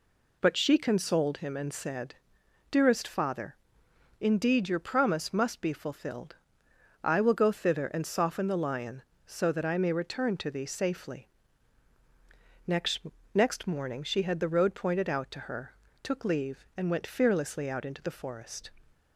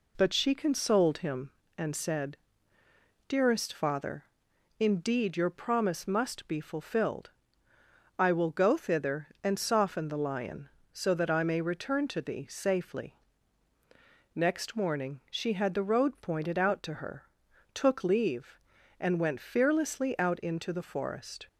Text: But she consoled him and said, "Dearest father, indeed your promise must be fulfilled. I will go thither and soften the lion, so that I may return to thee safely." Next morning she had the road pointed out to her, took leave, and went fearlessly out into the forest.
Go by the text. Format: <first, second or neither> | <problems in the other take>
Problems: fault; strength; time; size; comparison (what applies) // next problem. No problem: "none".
second | says "Next" twice; at 13.3 s